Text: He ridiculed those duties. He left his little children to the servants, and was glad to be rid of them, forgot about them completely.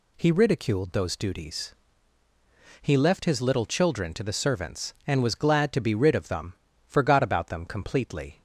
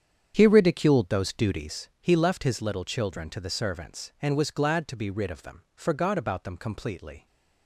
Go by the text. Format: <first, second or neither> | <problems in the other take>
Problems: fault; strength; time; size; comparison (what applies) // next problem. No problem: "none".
first | starts louder than the rest; strong; until 1.8 s; 8 dB